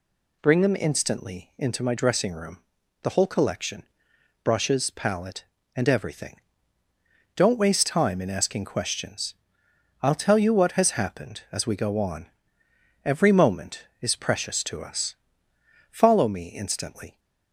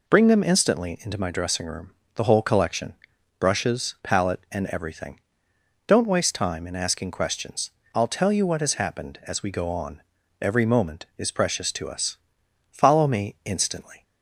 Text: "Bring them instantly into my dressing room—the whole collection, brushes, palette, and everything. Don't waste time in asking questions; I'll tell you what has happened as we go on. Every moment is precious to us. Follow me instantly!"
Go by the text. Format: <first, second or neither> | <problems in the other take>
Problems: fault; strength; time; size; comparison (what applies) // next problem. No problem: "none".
neither | none